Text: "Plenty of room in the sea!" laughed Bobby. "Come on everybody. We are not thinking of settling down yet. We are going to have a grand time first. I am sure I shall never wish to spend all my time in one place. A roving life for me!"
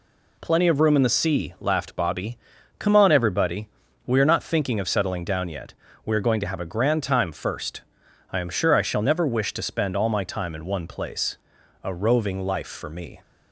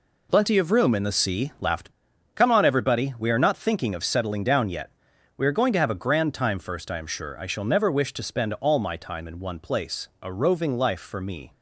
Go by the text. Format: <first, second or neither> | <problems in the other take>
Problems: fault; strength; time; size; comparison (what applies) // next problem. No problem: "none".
first | skips "Bobby"; at 2.1 s